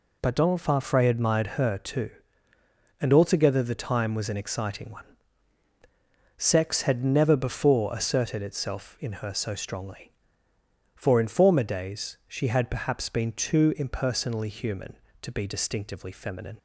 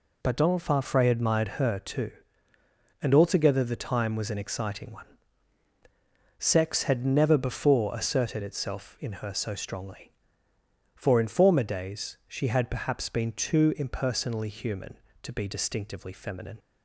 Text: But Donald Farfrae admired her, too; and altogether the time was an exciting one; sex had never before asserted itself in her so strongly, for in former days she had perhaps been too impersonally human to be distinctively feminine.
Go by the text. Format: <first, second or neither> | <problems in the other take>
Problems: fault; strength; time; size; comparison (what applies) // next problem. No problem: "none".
neither | none